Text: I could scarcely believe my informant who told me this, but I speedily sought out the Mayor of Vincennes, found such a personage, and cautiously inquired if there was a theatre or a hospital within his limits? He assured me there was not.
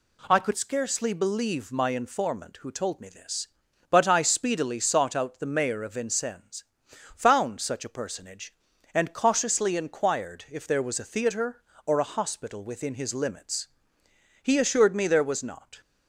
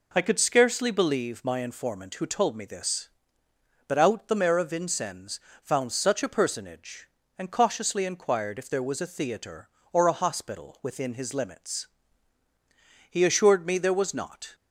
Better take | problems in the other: first | skips "I speedily sought"; at 3.9 s

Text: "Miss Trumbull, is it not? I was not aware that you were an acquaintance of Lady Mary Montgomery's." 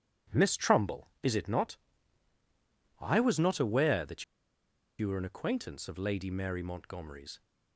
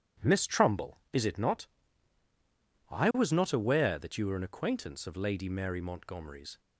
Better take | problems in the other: second | pauses between "that" and "you"; noticeable; at 4.2 s; 0.76 s long

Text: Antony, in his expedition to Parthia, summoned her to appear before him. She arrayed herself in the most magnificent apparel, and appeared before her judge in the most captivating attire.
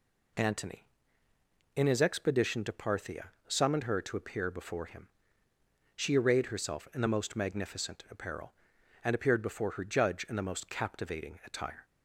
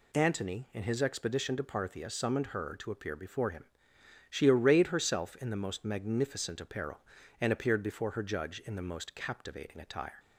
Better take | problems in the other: neither | none

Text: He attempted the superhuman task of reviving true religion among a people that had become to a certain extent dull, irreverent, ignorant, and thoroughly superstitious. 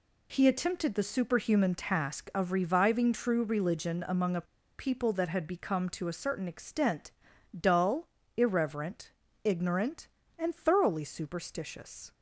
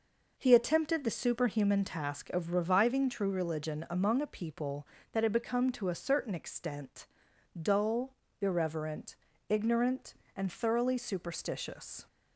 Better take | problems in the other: second | pauses between "a" and "people"; slight; at 4.4 s; 0.33 s long // pauses between "extent" and "dull"; at 7.1 s; 0.42 s long; noticeable in the second

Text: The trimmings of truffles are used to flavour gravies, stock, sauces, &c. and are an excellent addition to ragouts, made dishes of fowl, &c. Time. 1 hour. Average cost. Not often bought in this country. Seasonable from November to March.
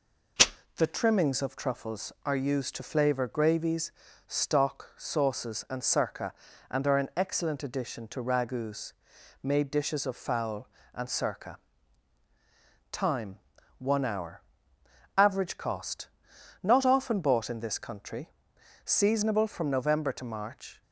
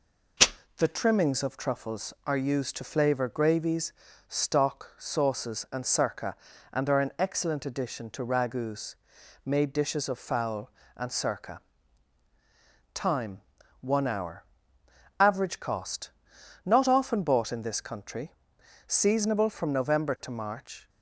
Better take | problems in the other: neither | none

